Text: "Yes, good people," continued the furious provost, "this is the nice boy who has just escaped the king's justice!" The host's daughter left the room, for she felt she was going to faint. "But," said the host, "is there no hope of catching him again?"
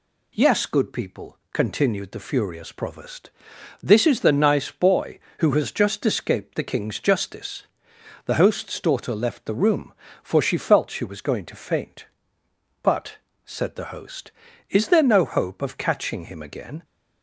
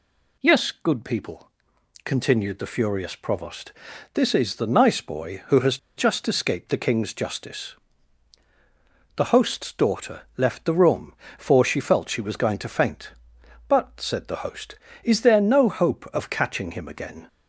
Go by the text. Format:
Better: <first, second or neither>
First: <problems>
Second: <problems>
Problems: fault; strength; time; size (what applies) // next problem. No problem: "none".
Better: first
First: none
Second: pauses between "has" and "just"; slight; at 5.7 s; 0.19 s long // pauses between "daughter" and "left"; slight; at 10.2 s; 0.16 s long